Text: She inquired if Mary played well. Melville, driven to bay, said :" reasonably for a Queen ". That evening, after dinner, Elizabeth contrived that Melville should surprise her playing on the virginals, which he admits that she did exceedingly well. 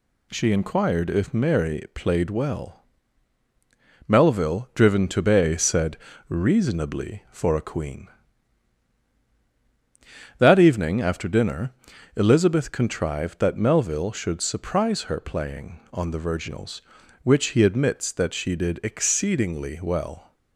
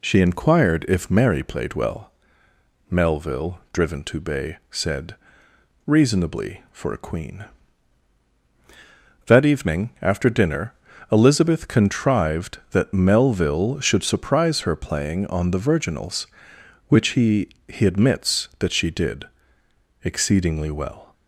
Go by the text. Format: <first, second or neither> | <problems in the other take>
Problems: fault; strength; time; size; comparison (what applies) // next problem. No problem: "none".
first | says "he" twice; at 17.6 s // pauses between "did" and "exceedingly"; noticeable; at 19.2 s; 0.78 s long